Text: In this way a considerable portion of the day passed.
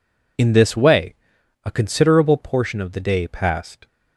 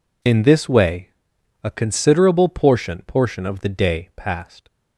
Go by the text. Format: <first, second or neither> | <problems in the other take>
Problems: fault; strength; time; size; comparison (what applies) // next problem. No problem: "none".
first | pauses between "way" and "a"; noticeable; at 1.0 s; 0.56 s long; noticeable in the first // says "portion" twice; at 3.0 s